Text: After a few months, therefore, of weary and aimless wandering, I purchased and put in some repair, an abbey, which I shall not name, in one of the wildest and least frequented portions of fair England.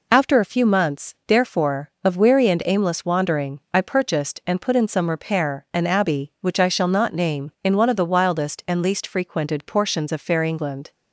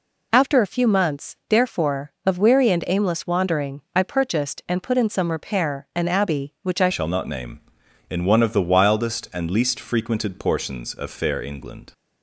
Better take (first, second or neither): first